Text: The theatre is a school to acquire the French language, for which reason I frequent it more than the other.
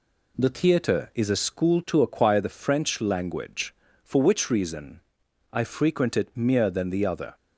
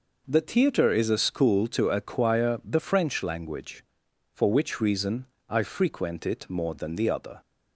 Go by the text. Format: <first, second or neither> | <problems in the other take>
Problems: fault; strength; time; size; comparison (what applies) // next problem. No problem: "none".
second | pauses between "reason" and "I"; noticeable; at 5.0 s; 0.50 s long; slight in the second // says "mere" for "more"; at 6.3 s